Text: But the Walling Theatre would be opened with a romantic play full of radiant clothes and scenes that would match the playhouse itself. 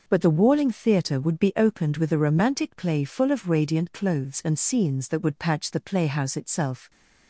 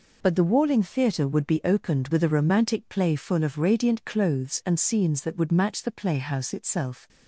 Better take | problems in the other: second | says "patch" for "match"; at 5.3 s

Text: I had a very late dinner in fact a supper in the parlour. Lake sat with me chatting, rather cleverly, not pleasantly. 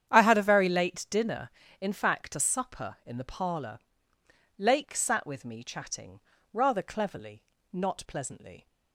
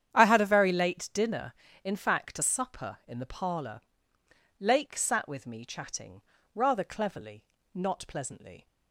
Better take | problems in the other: neither | starts louder than the rest; strong; the same in both

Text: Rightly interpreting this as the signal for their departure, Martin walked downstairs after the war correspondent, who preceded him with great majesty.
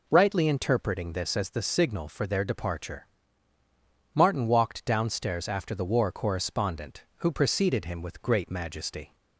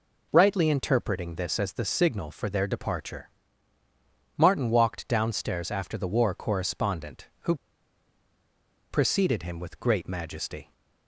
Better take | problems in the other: first | pauses between "who" and "preceded"; strong; at 7.5 s; 1.3 s long

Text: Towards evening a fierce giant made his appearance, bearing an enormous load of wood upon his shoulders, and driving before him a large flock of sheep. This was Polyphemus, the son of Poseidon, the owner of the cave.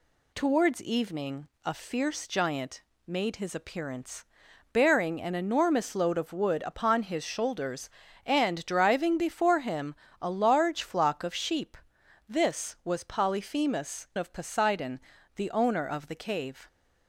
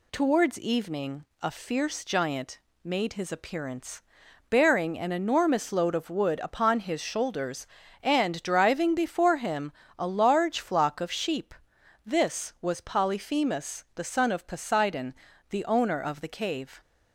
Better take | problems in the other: second | pauses between "evening" and "a"; slight; at 1.4 s; 0.16 s long; slight in the second // pauses between "giant" and "made"; slight; at 2.8 s; 0.26 s long; slight in the second // pauses between "him" and "a"; slight; at 9.9 s; 0.28 s long; slight in the second // skips "the son"; at 14.1 s

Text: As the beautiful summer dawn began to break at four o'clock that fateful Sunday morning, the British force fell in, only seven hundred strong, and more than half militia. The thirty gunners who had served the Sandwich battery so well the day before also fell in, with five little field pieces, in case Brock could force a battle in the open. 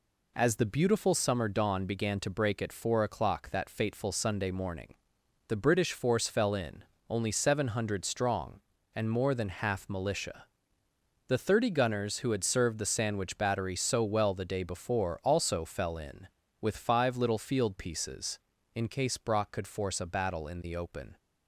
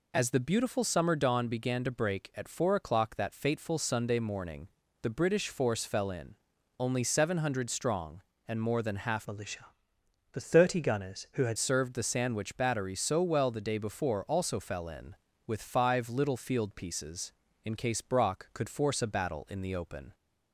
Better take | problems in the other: first | changes voice from "militia" to "had"; from 9.2 to 11.5 s; 2.3 s long

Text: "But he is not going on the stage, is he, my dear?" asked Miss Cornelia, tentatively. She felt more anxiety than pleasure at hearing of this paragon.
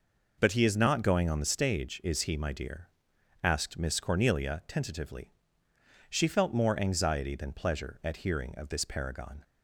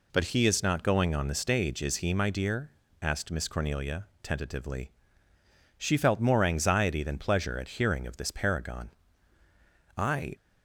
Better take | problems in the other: first | goes on to say "I"; slight; from 9.9 s on; 0.38 s long

